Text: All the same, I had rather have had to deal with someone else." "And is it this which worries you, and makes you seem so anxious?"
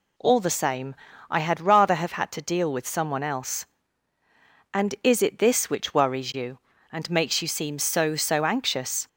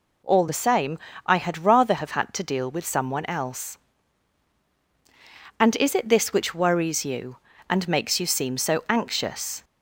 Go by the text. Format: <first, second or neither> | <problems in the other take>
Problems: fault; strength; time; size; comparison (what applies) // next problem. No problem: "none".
second | says "so" twice; at 8.1 s